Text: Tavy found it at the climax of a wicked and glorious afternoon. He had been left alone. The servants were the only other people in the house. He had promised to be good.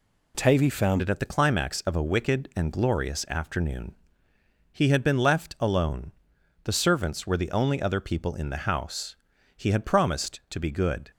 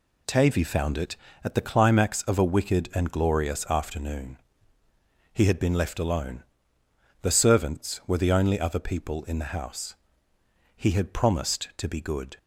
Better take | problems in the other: second | changes voice at "it"; from 1.0 s on; 10.1 s long

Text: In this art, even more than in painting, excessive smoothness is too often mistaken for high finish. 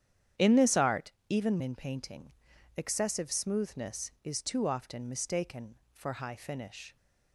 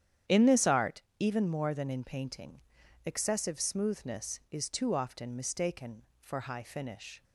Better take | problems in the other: second | starts louder than the rest; strong; until 1.5 s; 9.5 dB; strong in the second // skips "more than"; at 1.5 s

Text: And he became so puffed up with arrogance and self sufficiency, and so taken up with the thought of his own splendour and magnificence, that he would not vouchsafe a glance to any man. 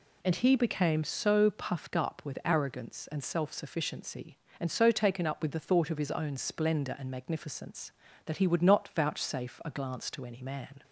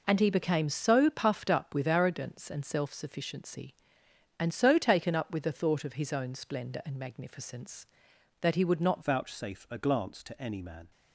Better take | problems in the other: first | changes voice at "vouchsafe"; from 9.0 s on; 1.8 s long

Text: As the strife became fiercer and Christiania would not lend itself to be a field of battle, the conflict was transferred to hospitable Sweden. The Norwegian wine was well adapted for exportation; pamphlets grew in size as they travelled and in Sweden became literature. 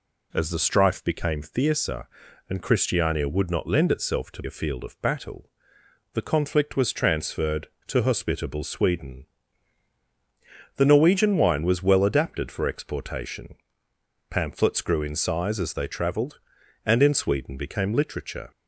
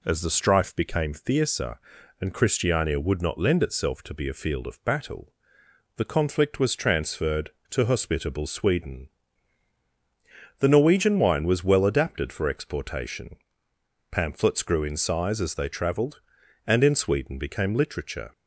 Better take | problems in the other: second | skips "be"; at 4.4 s

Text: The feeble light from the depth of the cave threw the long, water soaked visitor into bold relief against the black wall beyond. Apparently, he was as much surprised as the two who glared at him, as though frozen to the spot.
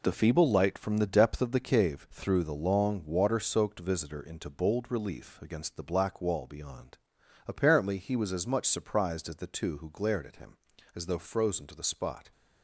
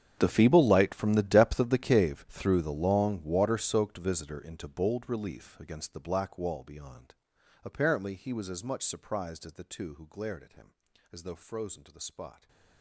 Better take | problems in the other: first | gets quieter; strong; throughout; 20 dB

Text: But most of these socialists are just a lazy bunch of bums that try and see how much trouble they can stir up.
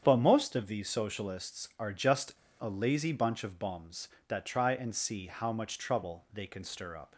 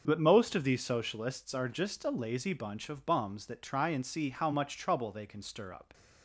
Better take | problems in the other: second | starts louder than the rest; strong; until 1.0 s; 8 dB // pauses between "just" and "a"; slight; at 2.3 s; 0.25 s long

